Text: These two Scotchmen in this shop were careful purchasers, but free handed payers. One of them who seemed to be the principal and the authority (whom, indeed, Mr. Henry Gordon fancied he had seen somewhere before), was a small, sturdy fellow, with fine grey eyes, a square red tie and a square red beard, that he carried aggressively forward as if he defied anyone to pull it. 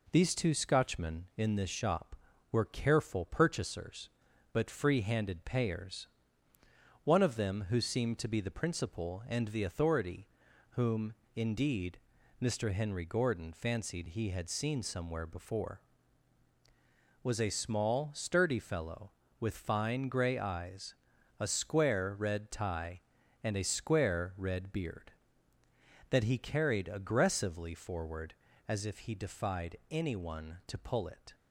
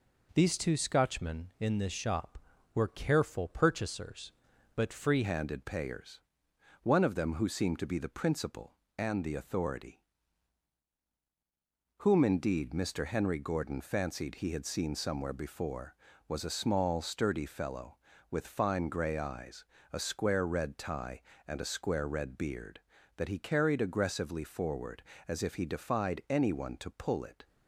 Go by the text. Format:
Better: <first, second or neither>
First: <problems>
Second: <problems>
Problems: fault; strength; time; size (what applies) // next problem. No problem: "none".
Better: first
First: none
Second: changes voice at "handed"; from 5.2 s on; 22.2 s long